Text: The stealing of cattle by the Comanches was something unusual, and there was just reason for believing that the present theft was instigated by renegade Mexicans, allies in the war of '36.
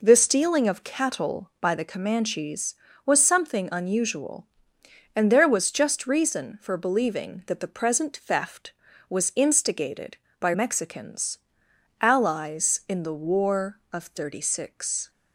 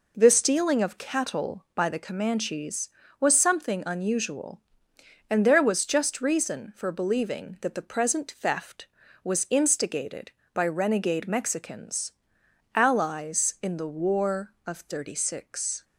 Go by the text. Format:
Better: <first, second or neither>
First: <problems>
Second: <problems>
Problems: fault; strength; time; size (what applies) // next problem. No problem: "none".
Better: second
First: skips "renegade"; at 10.5 s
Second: none